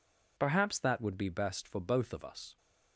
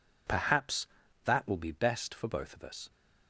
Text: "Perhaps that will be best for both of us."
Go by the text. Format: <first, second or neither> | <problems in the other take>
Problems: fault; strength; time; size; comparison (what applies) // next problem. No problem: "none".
second | says "would" for "will"; at 1.0 s